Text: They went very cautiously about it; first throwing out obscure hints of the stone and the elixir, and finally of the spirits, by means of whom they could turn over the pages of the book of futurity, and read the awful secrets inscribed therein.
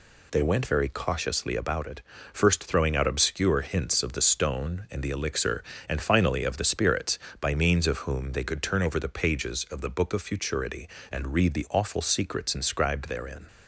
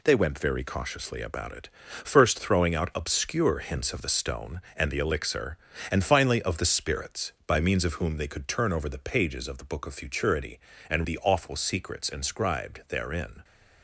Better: first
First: none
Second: skips "read"; at 11.0 s

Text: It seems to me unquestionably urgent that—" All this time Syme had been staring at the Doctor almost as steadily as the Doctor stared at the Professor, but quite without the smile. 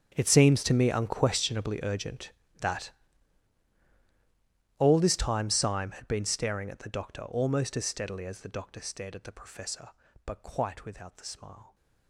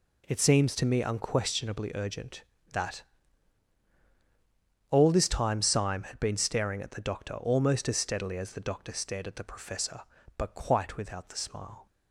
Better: second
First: gets quieter; strong; throughout; 18.5 dB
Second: none

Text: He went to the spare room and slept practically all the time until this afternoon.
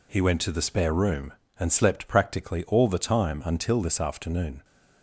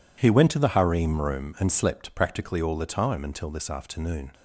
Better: first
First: none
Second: says "harem" for "spare"; at 0.7 s

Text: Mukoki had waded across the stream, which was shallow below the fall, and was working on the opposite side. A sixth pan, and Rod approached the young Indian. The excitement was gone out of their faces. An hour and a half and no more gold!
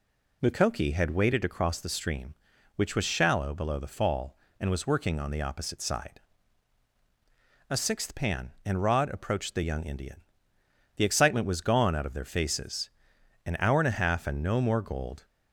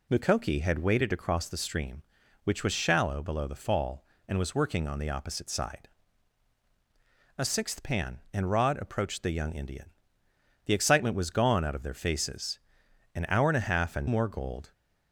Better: first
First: none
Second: skips "no"; at 14.0 s

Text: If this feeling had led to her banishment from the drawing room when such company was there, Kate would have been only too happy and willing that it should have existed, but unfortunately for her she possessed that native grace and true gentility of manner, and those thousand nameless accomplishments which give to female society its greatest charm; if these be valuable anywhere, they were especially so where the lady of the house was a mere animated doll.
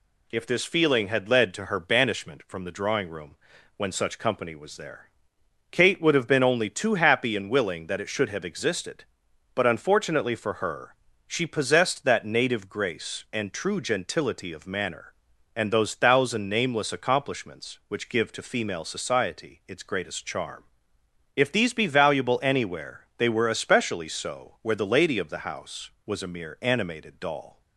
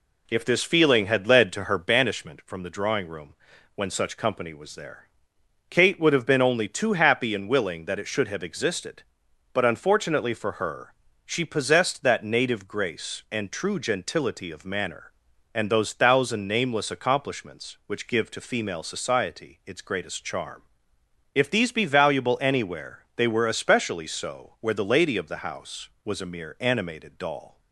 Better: first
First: pauses between "room" and "when"; at 3.3 s; 0.40 s long // pauses between "her" and "she"; slight; at 10.9 s; 0.34 s long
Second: starts louder than the rest; slight; until 2.0 s; 2 dB // pauses between "room" and "when"; at 3.3 s; 0.40 s long // pauses between "her" and "she"; slight; at 10.9 s; 0.34 s long

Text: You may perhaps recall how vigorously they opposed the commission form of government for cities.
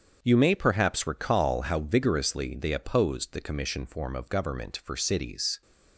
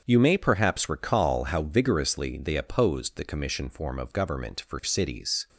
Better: neither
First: starts louder than the rest; strong; until 1.2 s; 7.5 dB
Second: starts louder than the rest; strong; until 1.0 s; 7.5 dB

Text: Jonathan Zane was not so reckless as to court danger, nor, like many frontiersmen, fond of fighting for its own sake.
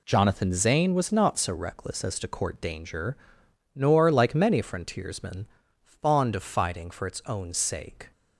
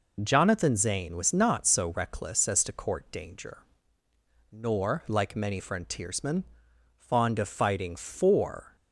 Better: first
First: none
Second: stops before "its own sake"; at 8.7 s

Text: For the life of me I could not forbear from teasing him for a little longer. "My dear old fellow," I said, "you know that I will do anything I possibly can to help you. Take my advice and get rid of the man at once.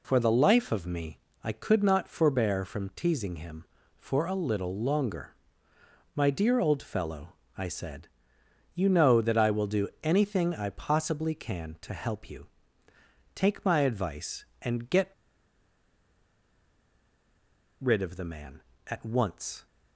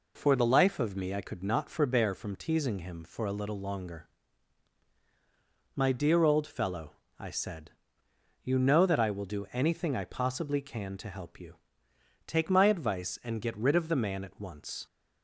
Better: second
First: pauses between "me" and "I"; slight; at 1.1 s; 0.26 s long // pauses between "do" and "anything"; slight; at 9.8 s; 0.16 s long // pauses between "get" and "rid"; strong; at 15.0 s; 2.7 s long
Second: none

